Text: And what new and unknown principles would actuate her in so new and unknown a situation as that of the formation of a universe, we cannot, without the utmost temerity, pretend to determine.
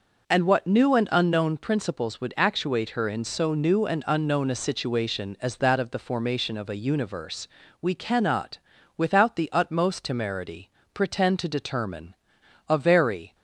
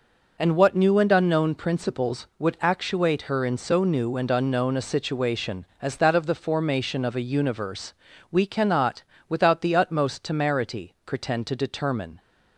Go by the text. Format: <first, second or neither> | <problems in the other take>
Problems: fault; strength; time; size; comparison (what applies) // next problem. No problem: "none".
second | goes on to say "A very"; noticeable; from 12.6 s on; 0.66 s long